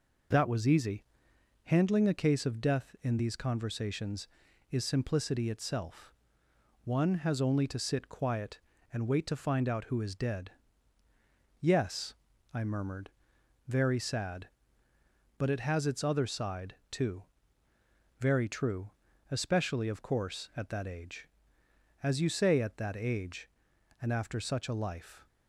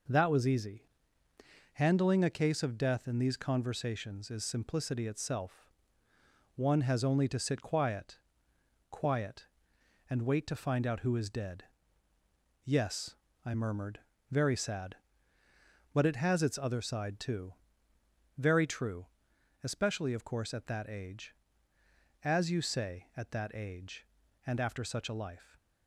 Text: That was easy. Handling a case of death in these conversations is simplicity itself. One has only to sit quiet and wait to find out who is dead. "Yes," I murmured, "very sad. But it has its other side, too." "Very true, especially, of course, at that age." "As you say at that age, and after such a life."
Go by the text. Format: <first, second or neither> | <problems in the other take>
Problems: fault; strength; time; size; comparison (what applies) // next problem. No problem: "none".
first | says "quiet" twice; at 8.8 s